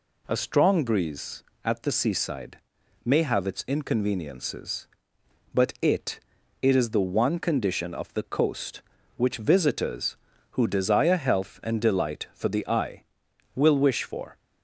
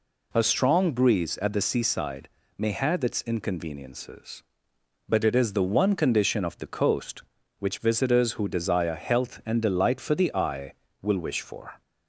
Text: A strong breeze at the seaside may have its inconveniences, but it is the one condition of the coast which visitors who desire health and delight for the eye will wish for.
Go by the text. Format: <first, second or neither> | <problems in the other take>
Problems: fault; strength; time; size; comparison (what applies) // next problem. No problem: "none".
second | pauses between "seaside" and "may"; noticeable; at 2.5 s; 0.46 s long; slight in the second // says "it" twice; at 6.6 s